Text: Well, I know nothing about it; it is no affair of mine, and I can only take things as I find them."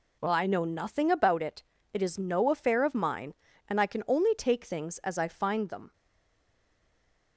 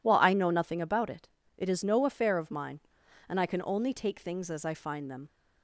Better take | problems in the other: second | stays silent after the last word; noticeable; from 5.9 s on; 1.4 s long

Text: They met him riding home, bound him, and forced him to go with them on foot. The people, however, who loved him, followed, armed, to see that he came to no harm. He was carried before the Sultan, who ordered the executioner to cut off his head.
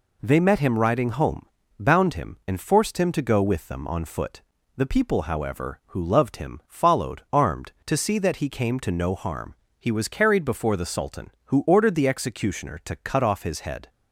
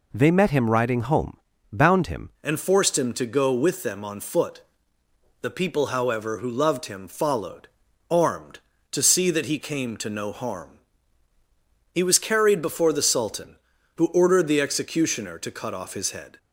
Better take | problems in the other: first | changes voice at "and"; from 2.4 s on; 13.9 s long

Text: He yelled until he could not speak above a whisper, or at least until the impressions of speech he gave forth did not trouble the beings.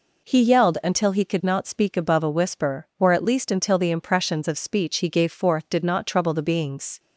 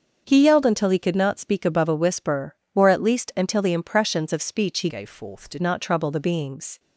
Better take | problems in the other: first | starts louder than the rest; until 1.2 s; 6.5 dB // changes voice from "gave" to "did"; from 4.8 to 5.6 s; 0.8 s long

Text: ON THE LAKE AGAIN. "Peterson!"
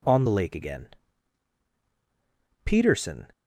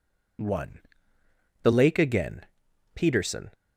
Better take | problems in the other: first | says "One" for "ON"; at 0.4 s

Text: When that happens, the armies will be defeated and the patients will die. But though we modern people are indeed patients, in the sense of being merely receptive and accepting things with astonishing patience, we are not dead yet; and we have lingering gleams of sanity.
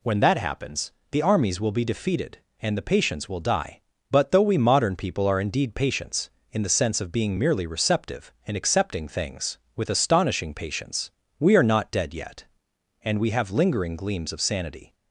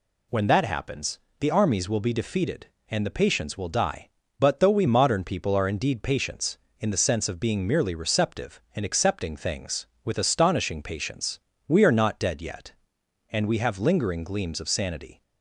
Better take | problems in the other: neither | none

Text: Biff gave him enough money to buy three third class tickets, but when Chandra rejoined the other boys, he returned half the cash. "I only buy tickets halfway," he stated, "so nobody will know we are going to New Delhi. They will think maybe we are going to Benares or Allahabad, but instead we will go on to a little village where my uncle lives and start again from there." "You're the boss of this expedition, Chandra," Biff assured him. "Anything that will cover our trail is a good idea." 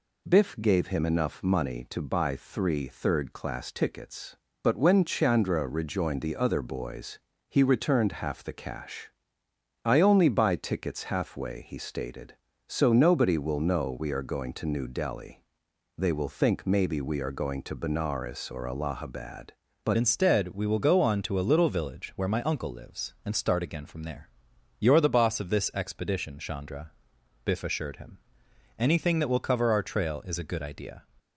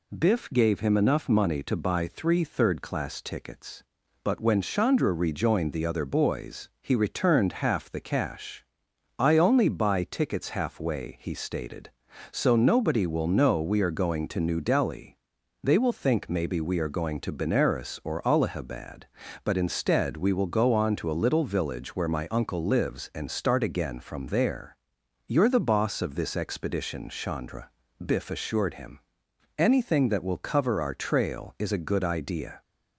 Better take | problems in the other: second | changes voice at "instead"; from 19.9 s on; 11.1 s long

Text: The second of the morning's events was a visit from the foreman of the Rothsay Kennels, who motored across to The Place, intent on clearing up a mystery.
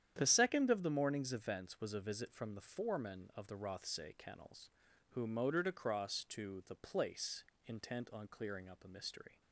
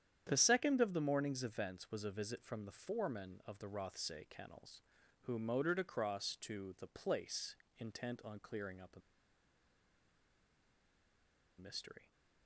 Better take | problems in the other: first | starts louder than the rest; strong; until 1.2 s; 9.5 dB; strong in the first // pauses between "a" and "mystery"; strong; at 8.9 s; 2.5 s long

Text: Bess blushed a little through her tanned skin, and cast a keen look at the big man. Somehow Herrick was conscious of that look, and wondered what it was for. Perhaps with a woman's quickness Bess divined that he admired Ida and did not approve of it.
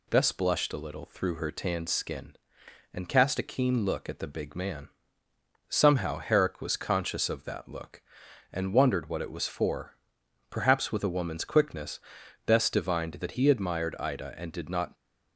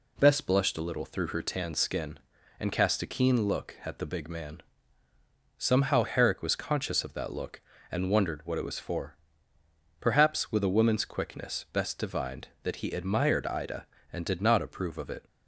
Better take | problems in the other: second | pauses between "quickness" and "Bess"; noticeable; at 11.9 s; 0.46 s long // stops before "approve of it"; at 14.9 s

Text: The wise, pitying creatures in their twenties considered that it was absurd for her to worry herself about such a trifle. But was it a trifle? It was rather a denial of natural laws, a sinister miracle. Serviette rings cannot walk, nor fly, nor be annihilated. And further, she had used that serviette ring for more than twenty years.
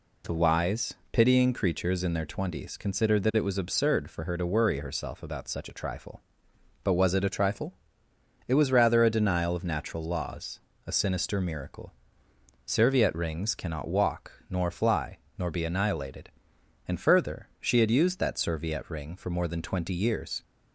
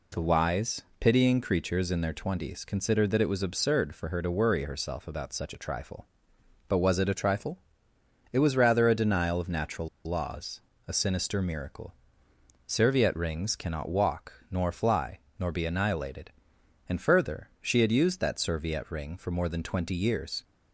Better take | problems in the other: first | pauses between "natural" and "laws"; slight; at 9.8 s; 0.16 s long

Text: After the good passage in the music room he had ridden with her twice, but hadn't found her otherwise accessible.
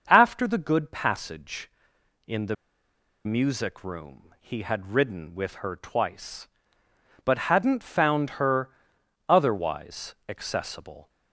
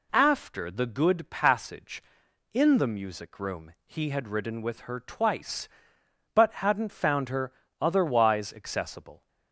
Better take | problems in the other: second | starts louder than the rest; until 1.0 s; 6.5 dB // pauses between "the" and "music"; noticeable; at 2.5 s; 0.71 s long // pauses between "her" and "otherwise"; noticeable; at 8.7 s; 0.58 s long; slight in the second

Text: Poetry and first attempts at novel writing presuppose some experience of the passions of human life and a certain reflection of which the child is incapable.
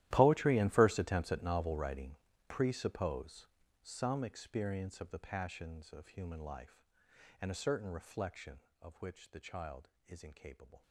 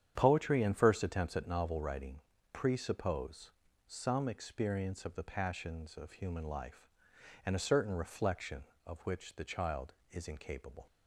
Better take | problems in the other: second | gets quieter; strong; throughout; 19 dB // starts louder than the rest; strong; until 1.1 s; 14 dB; strong in the second // pauses between "writing" and "presuppose"; slight; at 2.1 s; 0.34 s long; slight in the second // pauses between "presuppose" and "some"; slight; at 3.4 s; 0.36 s long; slight in the second

